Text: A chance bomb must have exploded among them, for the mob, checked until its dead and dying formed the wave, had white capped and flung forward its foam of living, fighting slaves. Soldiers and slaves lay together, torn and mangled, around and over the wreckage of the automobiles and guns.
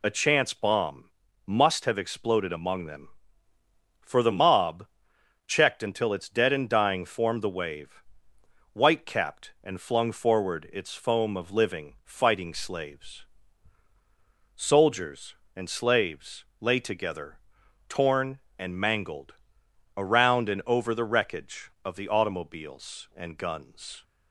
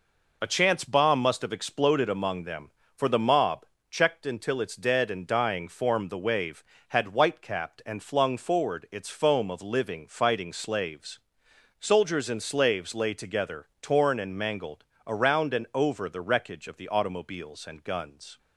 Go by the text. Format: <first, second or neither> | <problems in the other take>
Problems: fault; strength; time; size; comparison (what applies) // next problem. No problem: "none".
second | pauses between "bomb" and "must"; at 1.0 s; 0.38 s long // skips "had"; at 8.3 s // pauses between "slaves" and "lay"; slight; at 16.4 s; 0.16 s long